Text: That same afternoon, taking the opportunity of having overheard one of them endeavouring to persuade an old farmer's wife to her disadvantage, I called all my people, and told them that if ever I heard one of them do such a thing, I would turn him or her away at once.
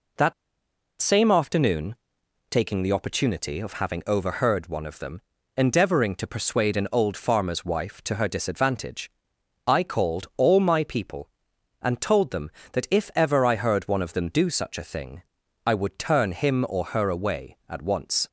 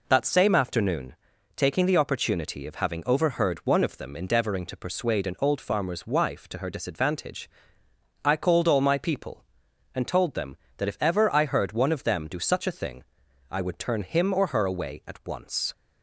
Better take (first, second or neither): second